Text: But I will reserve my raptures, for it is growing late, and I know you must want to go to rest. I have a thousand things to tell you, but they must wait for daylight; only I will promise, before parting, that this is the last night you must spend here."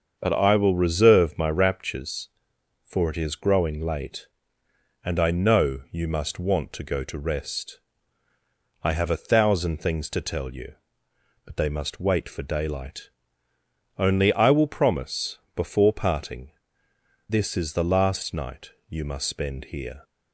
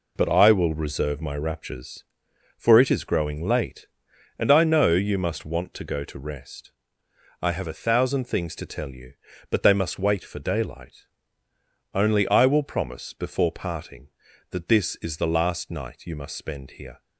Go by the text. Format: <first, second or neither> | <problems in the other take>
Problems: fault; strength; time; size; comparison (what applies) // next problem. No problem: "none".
second | starts louder than the rest; until 1.2 s; 6.5 dB // skips "that"; at 16.9 s // pauses between "night" and "you"; slight; at 18.7 s; 0.16 s long